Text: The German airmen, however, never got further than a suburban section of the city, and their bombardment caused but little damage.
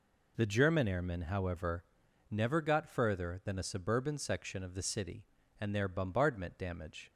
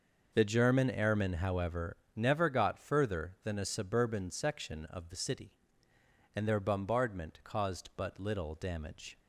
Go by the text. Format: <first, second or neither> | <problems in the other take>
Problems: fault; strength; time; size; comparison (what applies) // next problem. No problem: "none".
second | skips "caused but little"; at 6.5 s